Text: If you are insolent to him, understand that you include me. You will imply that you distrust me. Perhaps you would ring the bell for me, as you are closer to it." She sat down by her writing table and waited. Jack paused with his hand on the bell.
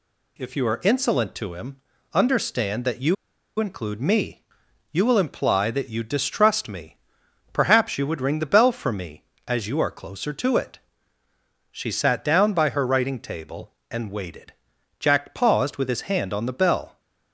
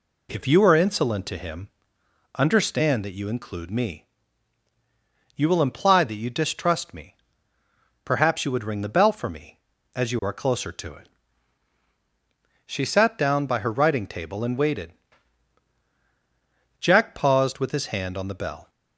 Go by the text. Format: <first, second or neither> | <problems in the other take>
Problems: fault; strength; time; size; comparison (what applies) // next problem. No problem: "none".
second | pauses between "you" and "include"; at 3.1 s; 0.43 s long